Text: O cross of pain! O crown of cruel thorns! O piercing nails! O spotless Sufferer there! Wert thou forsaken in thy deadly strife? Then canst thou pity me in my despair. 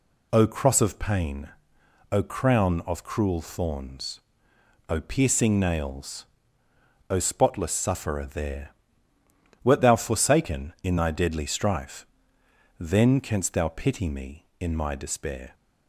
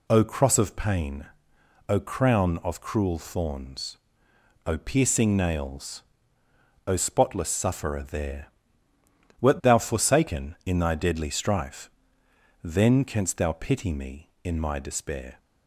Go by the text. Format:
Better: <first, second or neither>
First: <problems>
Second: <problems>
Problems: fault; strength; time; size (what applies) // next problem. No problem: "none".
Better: neither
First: none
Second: none